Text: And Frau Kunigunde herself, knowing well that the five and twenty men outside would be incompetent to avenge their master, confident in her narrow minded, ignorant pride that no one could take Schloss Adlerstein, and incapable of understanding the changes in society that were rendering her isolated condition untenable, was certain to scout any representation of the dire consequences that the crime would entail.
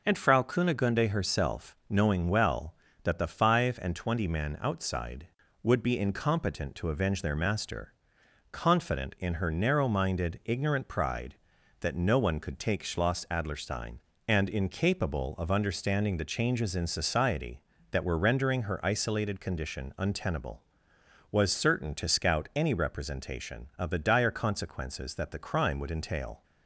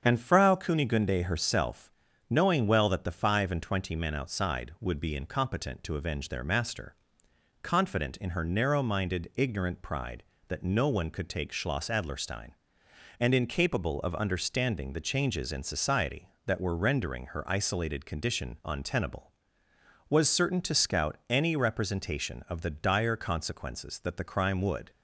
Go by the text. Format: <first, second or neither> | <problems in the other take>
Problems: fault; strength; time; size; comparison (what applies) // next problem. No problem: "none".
first | starts louder than the rest; strong; until 1.0 s; 7.5 dB // stops before "entail"; at 24.8 s